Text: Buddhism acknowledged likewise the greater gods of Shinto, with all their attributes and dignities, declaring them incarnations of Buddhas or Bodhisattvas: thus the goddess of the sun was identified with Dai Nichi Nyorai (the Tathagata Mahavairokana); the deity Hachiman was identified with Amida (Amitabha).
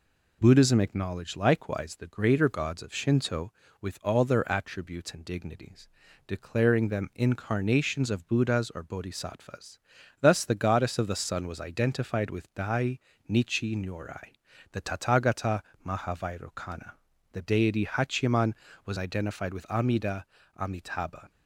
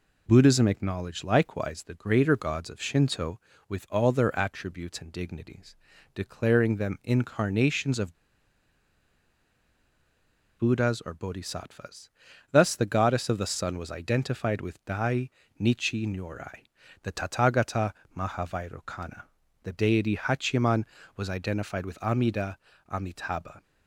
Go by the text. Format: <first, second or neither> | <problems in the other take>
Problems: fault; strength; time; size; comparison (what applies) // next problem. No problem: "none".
first | pauses between "of" and "Buddhas"; strong; at 8.1 s; 2.4 s long // pauses between "Dai" and "Nichi"; slight; at 15.3 s; 0.28 s long; slight in the first // pauses between "Tathagata" and "Mahavairokana"; slight; at 17.9 s; 0.20 s long; slight in the first